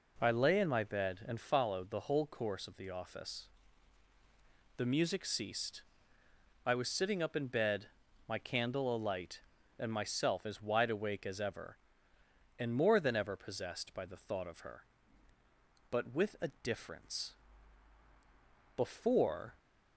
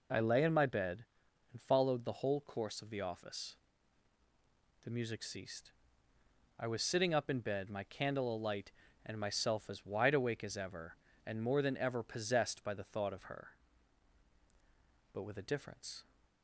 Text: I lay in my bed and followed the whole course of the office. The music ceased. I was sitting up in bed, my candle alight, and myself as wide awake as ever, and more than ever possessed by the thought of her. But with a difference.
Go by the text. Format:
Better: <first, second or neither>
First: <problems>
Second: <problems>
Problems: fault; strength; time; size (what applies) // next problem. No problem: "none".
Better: second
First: goes on to say "Before"; noticeable; from 18.7 s on; 0.82 s long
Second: none